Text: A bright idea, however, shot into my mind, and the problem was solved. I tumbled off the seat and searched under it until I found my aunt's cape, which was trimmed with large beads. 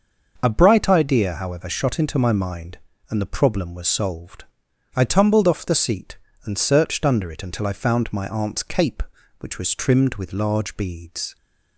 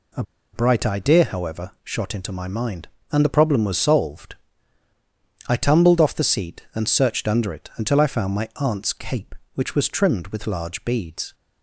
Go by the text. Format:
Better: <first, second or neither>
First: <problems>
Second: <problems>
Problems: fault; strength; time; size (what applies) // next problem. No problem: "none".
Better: first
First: none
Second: pauses between "A" and "bright"; slight; at 0.2 s; 0.31 s long